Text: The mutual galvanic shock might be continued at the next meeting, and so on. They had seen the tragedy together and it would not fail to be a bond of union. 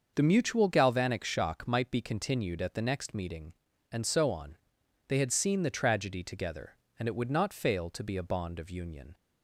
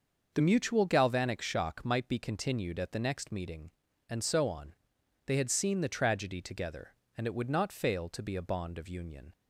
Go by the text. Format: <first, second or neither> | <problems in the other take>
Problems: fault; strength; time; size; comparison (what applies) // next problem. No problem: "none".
neither | starts louder than the rest; the same in both